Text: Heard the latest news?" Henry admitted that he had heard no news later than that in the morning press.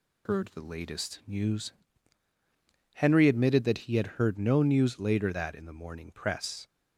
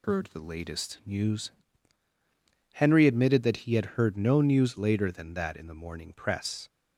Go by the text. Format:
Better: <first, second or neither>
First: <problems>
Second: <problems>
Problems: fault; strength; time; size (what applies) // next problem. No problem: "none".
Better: second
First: skips "than"; at 5.3 s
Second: none